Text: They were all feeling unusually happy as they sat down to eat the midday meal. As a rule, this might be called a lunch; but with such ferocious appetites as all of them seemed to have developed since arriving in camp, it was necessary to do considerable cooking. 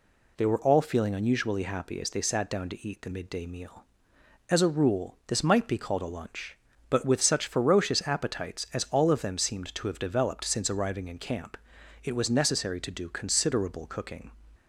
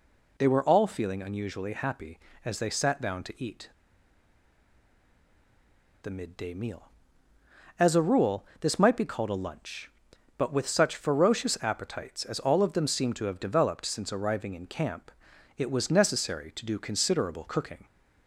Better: first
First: none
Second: pauses between "eat" and "the"; strong; at 3.6 s; 2.3 s long

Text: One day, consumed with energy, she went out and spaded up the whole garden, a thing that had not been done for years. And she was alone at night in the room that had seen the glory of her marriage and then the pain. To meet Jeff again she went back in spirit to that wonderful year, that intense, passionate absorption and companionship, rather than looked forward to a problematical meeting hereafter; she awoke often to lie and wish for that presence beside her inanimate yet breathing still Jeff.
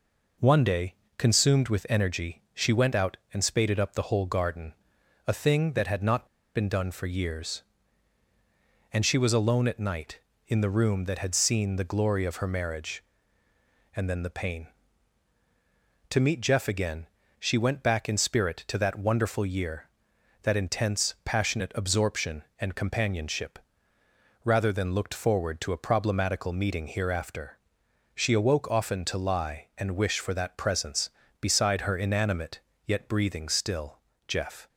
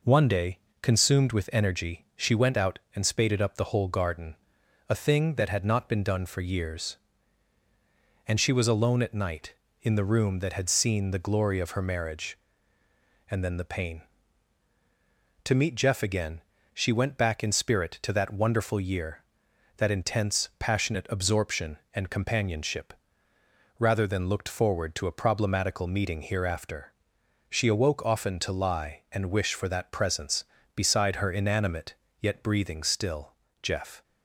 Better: second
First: pauses between "not" and "been"; slight; at 6.2 s; 0.30 s long // pauses between "again" and "she"; slight; at 17.0 s; 0.32 s long // pauses between "inanimate" and "yet"; slight; at 32.6 s; 0.26 s long // pauses between "still" and "Jeff"; slight; at 33.9 s; 0.28 s long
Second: pauses between "again" and "she"; slight; at 16.4 s; 0.32 s long // pauses between "inanimate" and "yet"; slight; at 31.9 s; 0.26 s long // pauses between "still" and "Jeff"; slight; at 33.3 s; 0.28 s long

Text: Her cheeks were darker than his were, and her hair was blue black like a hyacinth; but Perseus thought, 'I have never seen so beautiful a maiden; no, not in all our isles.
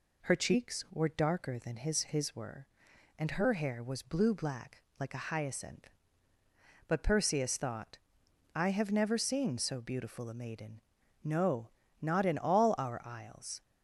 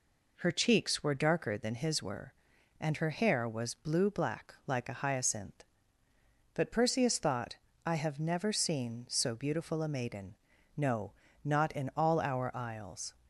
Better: second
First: says "his" twice; at 2.0 s // pauses between "black" and "like"; slight; at 4.8 s; 0.16 s long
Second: none

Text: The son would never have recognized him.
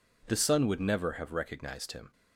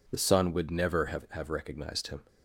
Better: first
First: none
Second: says "have" twice; at 1.3 s

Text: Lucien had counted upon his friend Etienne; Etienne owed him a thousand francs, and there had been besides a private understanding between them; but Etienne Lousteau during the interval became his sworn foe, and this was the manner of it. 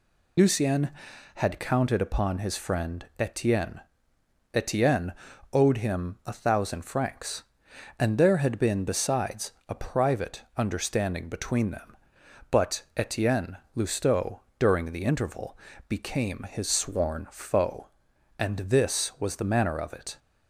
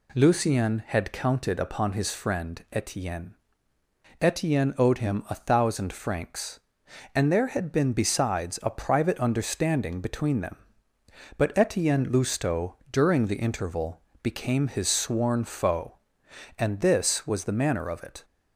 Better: second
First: loses the start of "Lucien"; at 0.3 s; 40 ms // pauses between "Etienne" and "owed"; at 5.1 s; 0.40 s long // pauses between "besides" and "a"; slight; at 9.5 s; 0.18 s long // pauses between "Etienne" and "Lousteau"; slight; at 13.5 s; 0.18 s long // pauses between "Lousteau" and "during"; slight; at 14.3 s; 0.22 s long // pauses between "interval" and "became"; slight; at 15.5 s; 0.32 s long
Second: pauses between "Lousteau" and "during"; slight; at 12.7 s; 0.16 s long // pauses between "interval" and "became"; slight; at 14.0 s; 0.20 s long

